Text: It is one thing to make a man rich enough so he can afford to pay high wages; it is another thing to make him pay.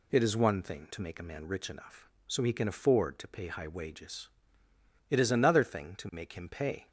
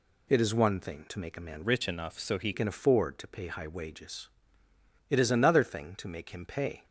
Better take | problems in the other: first | changes voice from "rich" to "he"; from 1.6 to 2.5 s; 0.9 s long

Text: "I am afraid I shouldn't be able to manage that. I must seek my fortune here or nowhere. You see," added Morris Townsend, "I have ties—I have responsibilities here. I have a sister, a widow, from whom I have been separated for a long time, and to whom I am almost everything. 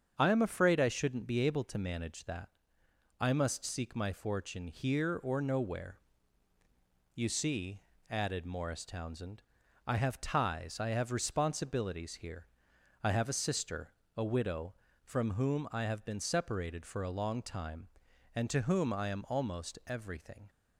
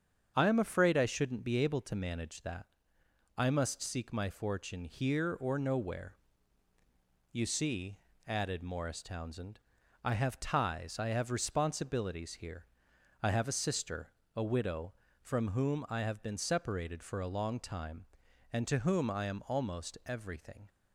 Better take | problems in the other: neither | starts louder than the rest; strong; the same in both

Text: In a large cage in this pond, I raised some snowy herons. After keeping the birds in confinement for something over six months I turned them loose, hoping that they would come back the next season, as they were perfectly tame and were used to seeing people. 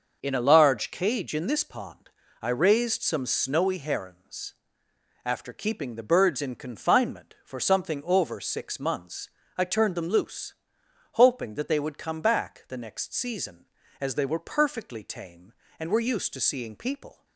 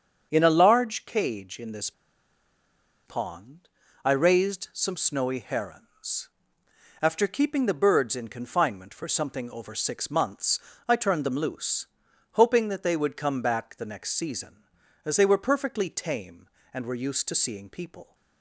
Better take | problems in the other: first | starts louder than the rest; strong; until 1.3 s; 7.5 dB; noticeable in the first // pauses between "this" and "pond"; at 1.9 s; 1.1 s long // pauses between "months" and "I"; slight; at 10.5 s; 0.30 s long; slight in the first

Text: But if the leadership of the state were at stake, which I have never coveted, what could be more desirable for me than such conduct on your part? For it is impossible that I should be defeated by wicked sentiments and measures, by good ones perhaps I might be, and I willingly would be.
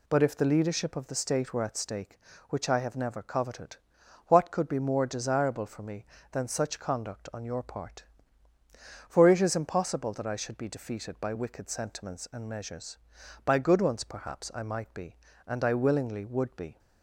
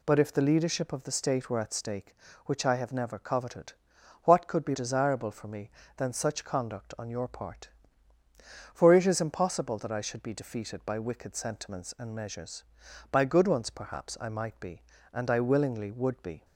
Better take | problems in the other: first | skips "more"; at 4.7 s

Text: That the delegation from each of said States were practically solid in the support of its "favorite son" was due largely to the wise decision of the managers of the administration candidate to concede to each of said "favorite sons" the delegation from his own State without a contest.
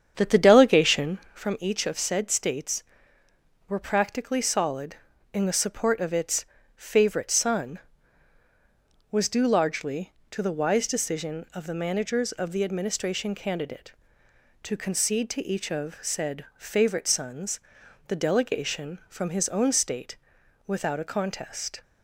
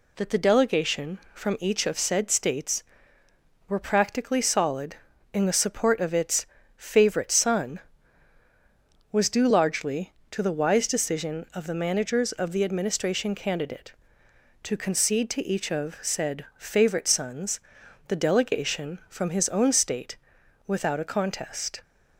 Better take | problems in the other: second | starts louder than the rest; strong; until 1.4 s; 8 dB // pauses between "its" and "favorite"; slight; at 6.4 s; 0.30 s long; slight in the second // pauses between "sons" and "the"; noticeable; at 17.5 s; 0.48 s long; noticeable in the second // pauses between "State" and "without"; noticeable; at 20.1 s; 0.52 s long; noticeable in the second

